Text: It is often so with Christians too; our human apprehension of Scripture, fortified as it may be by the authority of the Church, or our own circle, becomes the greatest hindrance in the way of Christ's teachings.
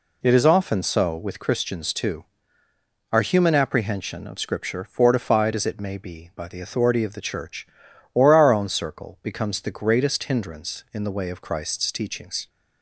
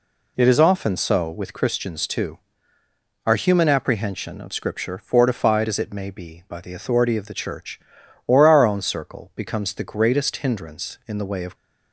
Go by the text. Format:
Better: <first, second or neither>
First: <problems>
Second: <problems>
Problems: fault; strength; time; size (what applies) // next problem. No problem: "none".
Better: first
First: none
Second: stops before "Christ's teachings"; at 11.5 s